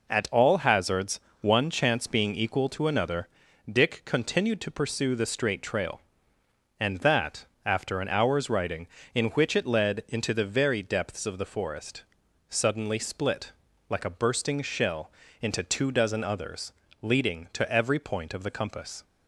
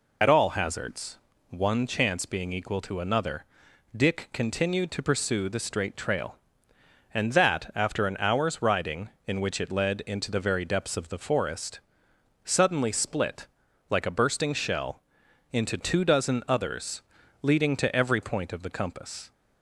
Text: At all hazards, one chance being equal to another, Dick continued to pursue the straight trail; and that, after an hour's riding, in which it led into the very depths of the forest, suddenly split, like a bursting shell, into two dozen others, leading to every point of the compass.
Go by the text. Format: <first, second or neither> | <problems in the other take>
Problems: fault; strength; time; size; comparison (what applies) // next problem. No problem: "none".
first | loses the start of "At"; at 0.2 s; 50 ms